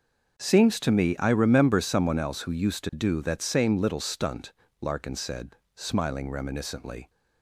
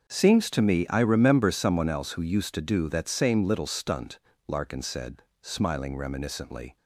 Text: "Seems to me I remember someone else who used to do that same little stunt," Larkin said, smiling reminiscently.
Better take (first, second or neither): neither